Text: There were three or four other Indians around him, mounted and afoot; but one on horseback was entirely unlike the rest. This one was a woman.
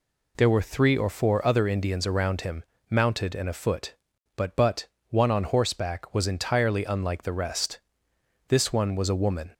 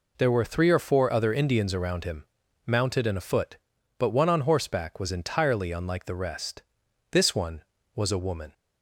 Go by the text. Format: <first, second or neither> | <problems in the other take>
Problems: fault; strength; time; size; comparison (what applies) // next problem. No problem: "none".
second | says "but" twice; at 4.5 s